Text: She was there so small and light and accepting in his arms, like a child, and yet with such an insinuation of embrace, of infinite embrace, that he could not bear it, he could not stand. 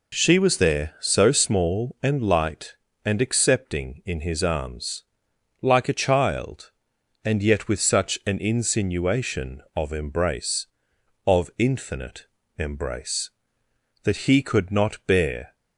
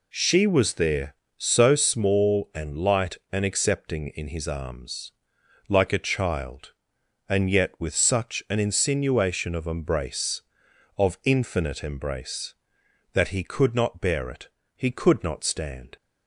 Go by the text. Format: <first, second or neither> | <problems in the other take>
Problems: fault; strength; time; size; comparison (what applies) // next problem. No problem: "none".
second | pauses between "infinite" and "embrace"; slight; at 12.2 s; 0.32 s long // stops before "it he could not stand"; at 15.5 s